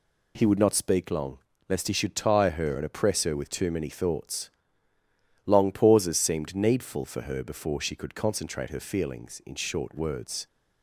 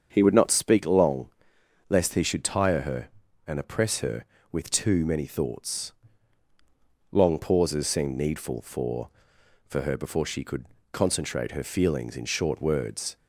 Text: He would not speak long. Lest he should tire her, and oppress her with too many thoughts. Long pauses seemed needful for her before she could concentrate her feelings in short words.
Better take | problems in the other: first | starts louder than the rest; strong; until 1.1 s; 7 dB // says "for" twice; at 9.6 s // pauses between "could" and "concentrate"; slight; at 10.6 s; 0.26 s long

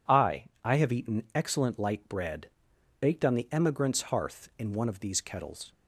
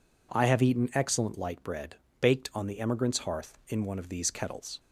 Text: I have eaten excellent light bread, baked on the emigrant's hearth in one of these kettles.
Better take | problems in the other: second | says "I" twice; at 0.6 s

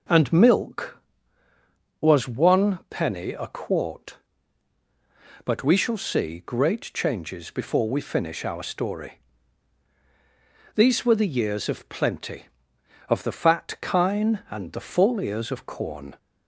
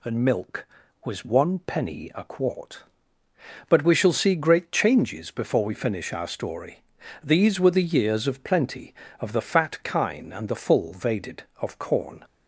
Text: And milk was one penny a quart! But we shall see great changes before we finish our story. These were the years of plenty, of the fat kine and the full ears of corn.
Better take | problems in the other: first | says "vaded" for "ears"; at 10.9 s

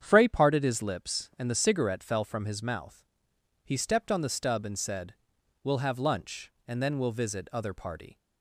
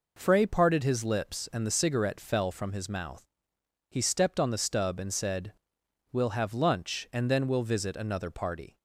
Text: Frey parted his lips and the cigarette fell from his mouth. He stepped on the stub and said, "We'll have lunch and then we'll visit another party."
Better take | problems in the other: second | starts louder than the rest; strong; until 1.0 s; 8.5 dB // says "other" for "another"; at 7.5 s

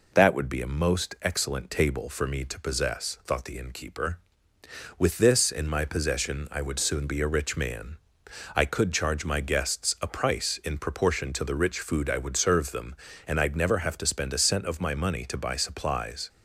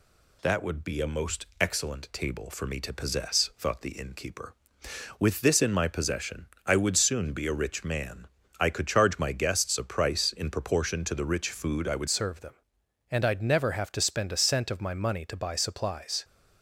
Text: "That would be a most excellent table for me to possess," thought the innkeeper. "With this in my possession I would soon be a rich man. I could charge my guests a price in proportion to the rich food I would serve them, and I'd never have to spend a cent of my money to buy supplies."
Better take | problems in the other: first | pauses between "possession" and "I"; slight; at 6.4 s; 0.20 s long // changes voice at "serve"; from 12.0 s on; 4.2 s long

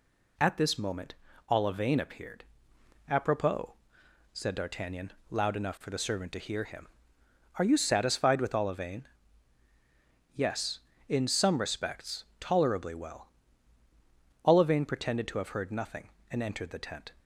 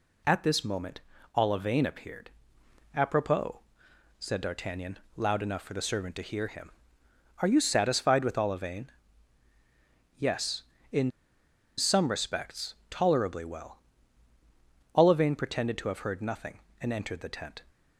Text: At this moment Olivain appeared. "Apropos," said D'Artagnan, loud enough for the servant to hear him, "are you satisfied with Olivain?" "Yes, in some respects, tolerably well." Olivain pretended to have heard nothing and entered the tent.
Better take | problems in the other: first | pauses between "moment" and "Olivain"; slight; at 0.9 s; 0.34 s long; slight in the first // pauses between "in" and "some"; noticeable; at 11.0 s; 0.68 s long

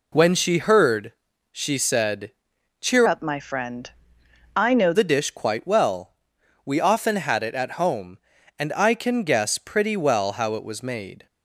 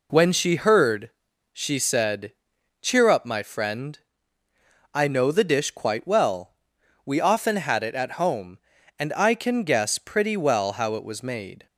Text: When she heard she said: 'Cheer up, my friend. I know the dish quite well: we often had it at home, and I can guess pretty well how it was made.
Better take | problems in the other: second | pauses between "heard" and "she"; at 1.1 s; 0.40 s long; also in the second // changes voice from "up" to "know"; from 3.0 to 4.9 s; 1.9 s long

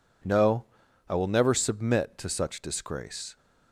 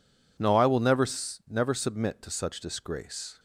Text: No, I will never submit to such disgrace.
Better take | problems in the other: first | says "never" twice; at 1.4 s

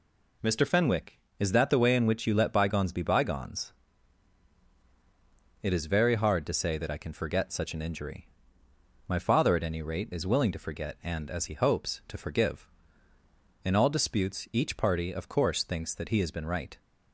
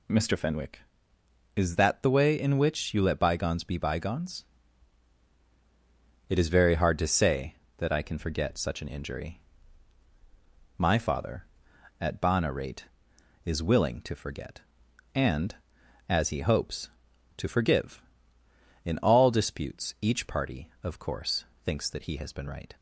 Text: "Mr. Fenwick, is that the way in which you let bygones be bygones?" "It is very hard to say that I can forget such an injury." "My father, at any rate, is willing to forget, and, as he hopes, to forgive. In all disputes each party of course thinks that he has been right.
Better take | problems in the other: first | says "bana" for "any"; at 12.1 s // pauses between "course" and "thinks"; slight; at 21.4 s; 0.18 s long

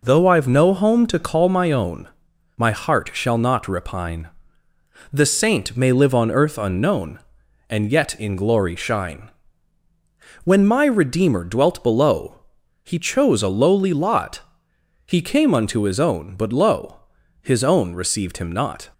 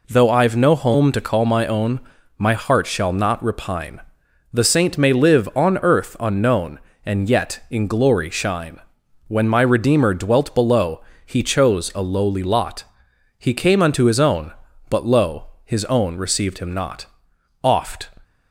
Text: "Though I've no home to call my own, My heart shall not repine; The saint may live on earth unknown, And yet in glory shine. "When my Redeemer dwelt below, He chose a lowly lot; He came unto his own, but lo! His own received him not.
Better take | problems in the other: first | goes on to say "Oft"; slight; from 17.6 s on; 0.46 s long

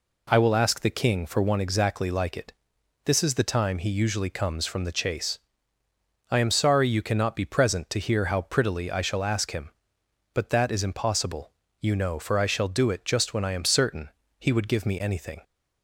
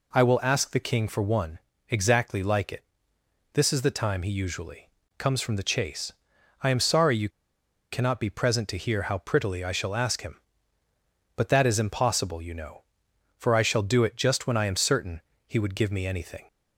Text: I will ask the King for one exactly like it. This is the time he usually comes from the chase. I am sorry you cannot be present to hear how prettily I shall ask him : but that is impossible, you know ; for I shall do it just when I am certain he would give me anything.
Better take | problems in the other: first | pauses between "one" and "exactly"; slight; at 1.5 s; 0.30 s long // pauses between "usually" and "comes"; slight; at 4.8 s; 0.30 s long // pauses between "you" and "cannot"; noticeable; at 7.2 s; 0.62 s long // pauses between "certain" and "he"; slight; at 15.1 s; 0.26 s long; slight in the first

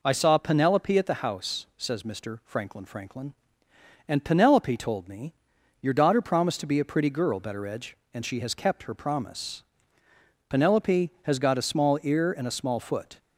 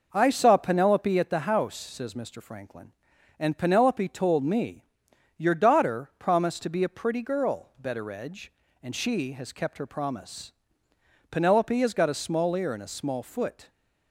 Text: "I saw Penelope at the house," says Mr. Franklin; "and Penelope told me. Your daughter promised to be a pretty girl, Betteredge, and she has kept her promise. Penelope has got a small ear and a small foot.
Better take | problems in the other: second | says "Franklin" twice; at 2.8 s

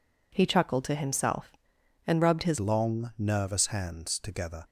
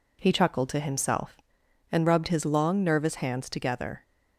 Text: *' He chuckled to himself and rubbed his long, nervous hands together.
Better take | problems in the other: second | changes voice at "long"; from 2.5 s on; 2.1 s long

